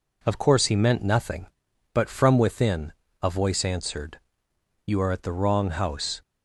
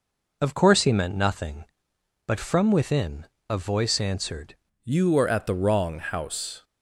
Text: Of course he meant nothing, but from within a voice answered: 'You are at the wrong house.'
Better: first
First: pauses between "within" and "a"; slight; at 2.9 s; 0.30 s long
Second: pauses between "within" and "a"; slight; at 3.2 s; 0.22 s long // changes voice at "You"; from 4.8 s on; 1.8 s long

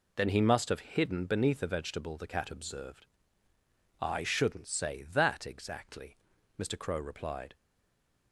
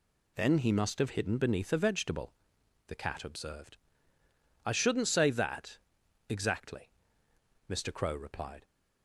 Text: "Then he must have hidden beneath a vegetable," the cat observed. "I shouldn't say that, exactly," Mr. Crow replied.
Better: second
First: stays silent after the last word; slight; from 7.5 s on; 0.8 s long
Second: none

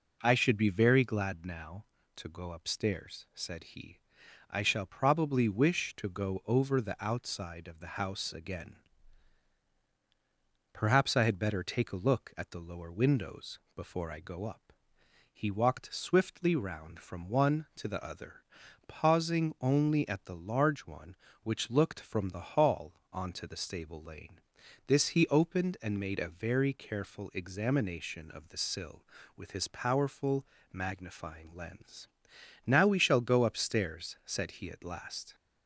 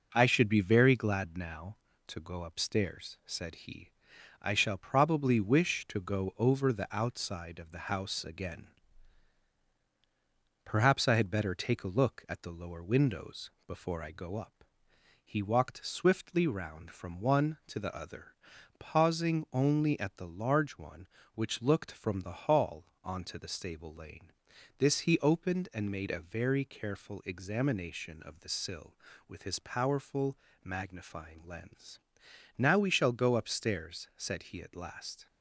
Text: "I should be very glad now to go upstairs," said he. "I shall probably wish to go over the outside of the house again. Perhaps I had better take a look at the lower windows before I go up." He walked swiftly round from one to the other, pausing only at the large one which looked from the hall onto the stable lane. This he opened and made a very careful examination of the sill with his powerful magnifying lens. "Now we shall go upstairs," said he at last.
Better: first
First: pauses between "windows" and "before"; slight; at 13.5 s; 0.16 s long // pauses between "hall" and "onto"; slight; at 22.9 s; 0.20 s long // pauses between "powerful" and "magnifying"; slight; at 30.4 s; 0.28 s long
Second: gets quieter; noticeable; throughout; 4 dB // pauses between "windows" and "before"; slight; at 13.5 s; 0.16 s long // pauses between "hall" and "onto"; slight; at 22.8 s; 0.20 s long // pauses between "powerful" and "magnifying"; slight; at 30.3 s; 0.28 s long

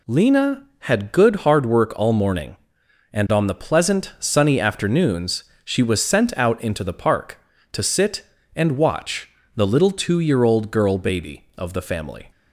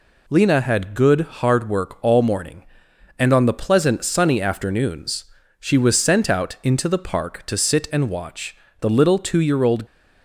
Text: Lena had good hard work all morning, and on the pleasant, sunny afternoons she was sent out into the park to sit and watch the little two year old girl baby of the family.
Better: first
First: pauses between "afternoons" and "she"; slight; at 5.4 s; 0.18 s long // pauses between "watch" and "the"; slight; at 9.2 s; 0.26 s long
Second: pauses between "afternoons" and "she"; slight; at 5.2 s; 0.34 s long // pauses between "watch" and "the"; slight; at 8.5 s; 0.24 s long // stops before "girl baby of the family"; at 9.8 s

